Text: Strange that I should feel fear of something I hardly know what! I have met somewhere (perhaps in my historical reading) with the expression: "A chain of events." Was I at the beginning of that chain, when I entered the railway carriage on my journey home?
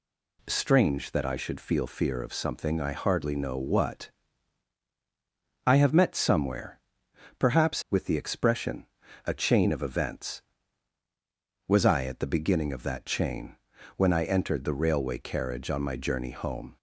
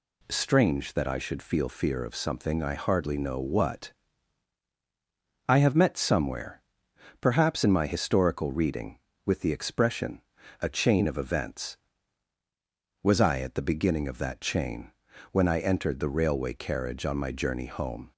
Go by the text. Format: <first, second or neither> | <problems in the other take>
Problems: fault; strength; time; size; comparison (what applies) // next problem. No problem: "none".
second | skips "in my historical reading"; at 7.8 s